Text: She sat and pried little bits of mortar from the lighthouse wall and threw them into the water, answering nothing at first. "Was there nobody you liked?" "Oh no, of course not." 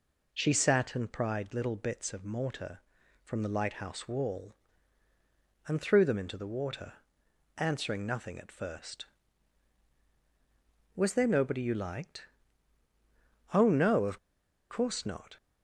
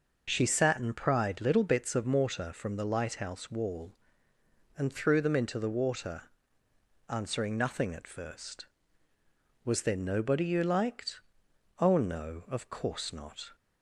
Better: second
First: pauses between "of" and "course"; noticeable; at 14.1 s; 0.52 s long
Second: none

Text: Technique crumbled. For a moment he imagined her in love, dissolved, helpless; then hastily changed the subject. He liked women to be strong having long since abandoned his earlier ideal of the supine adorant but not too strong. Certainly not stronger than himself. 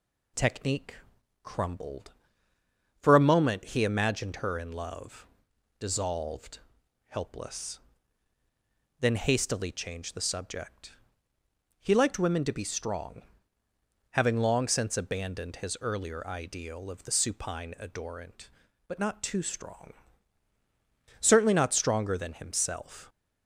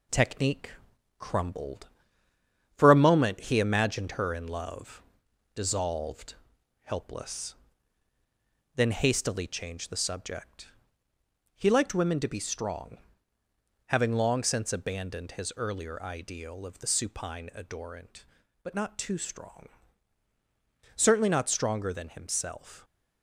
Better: first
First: pauses between "Technique" and "crumbled"; noticeable; at 0.9 s; 0.48 s long // pauses between "strong" and "having"; noticeable; at 13.2 s; 0.88 s long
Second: gets quieter; noticeable; throughout; 4 dB // pauses between "Technique" and "crumbled"; noticeable; at 0.7 s; 0.48 s long // pauses between "strong" and "having"; noticeable; at 12.9 s; 0.88 s long

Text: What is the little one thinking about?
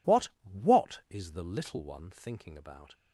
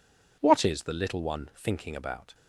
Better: second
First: says "What" twice; at 0.4 s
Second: none

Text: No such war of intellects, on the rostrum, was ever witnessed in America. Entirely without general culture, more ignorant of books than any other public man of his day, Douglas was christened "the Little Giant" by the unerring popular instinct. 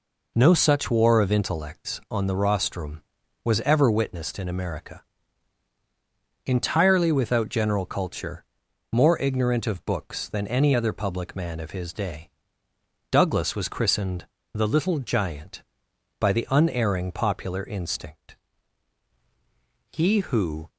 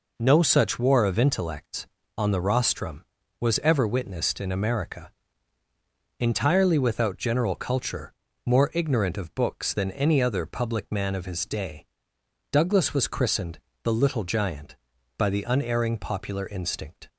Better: second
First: pauses between "christened" and "the"; slight; at 14.2 s; 0.26 s long // goes on to say "He who"; noticeable; from 19.9 s on; 0.76 s long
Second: pauses between "christened" and "the"; slight; at 13.5 s; 0.24 s long

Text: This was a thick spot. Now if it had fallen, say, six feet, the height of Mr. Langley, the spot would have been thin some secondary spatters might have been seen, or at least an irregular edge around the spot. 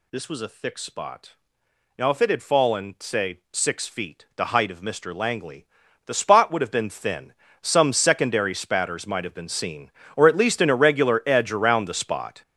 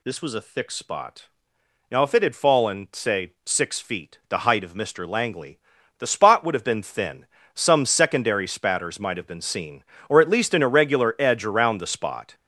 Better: second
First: gets louder; strong; throughout; 10 dB // pauses between "thin" and "some"; slight; at 7.3 s; 0.28 s long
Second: pauses between "thin" and "some"; slight; at 7.2 s; 0.28 s long

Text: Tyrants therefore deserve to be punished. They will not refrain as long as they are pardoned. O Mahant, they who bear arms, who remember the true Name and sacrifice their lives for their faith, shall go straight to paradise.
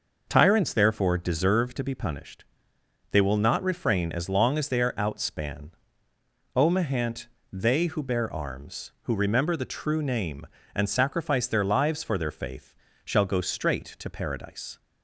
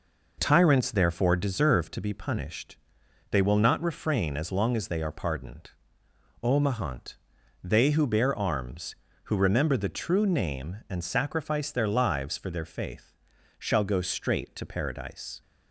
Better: second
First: says "outspan" for "pardoned"; at 4.9 s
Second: none

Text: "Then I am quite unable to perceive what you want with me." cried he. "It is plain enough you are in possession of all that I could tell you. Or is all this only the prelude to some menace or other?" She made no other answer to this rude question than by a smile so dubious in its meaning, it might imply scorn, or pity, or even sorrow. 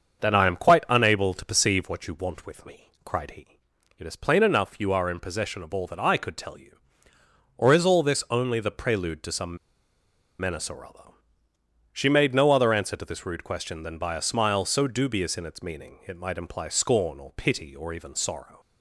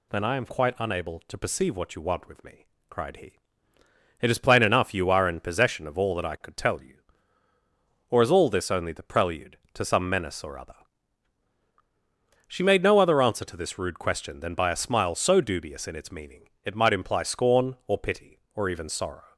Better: second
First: starts louder than the rest; until 1.2 s; 7 dB // pauses between "some" and "menace"; noticeable; at 9.5 s; 0.82 s long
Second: none

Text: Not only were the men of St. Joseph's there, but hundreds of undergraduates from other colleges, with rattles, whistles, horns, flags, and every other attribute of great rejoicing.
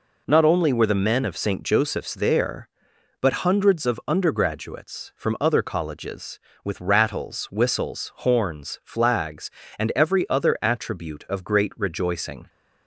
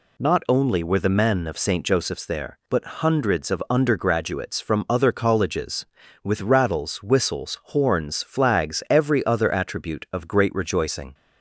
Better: first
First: none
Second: skips "and"; at 8.8 s

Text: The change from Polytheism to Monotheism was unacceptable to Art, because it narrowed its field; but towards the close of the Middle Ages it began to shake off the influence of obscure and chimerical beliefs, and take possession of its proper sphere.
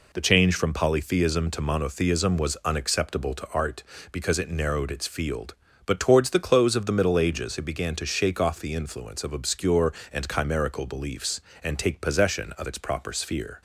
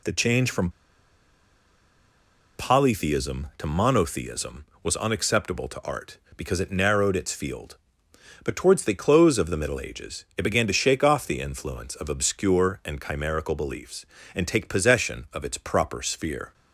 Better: first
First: none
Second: pauses between "from" and "Polytheism"; strong; at 0.6 s; 1.8 s long

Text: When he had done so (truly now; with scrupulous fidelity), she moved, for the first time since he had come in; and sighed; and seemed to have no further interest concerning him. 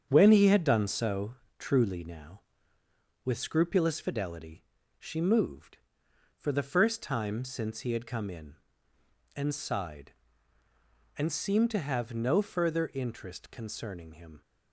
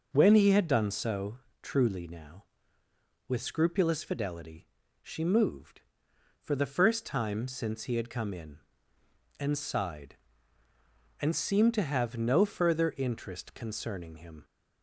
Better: second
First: gets quieter; noticeable; throughout; 6 dB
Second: none

